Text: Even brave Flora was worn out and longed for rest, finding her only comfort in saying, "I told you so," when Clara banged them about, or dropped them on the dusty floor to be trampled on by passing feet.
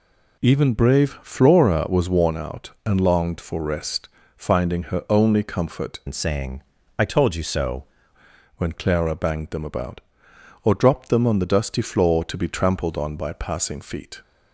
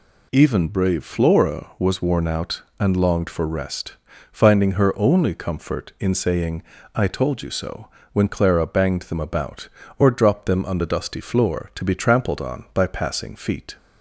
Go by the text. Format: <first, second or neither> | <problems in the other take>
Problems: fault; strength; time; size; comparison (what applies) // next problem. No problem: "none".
second | changes voice from "in" to "so"; from 6.0 to 7.8 s; 1.8 s long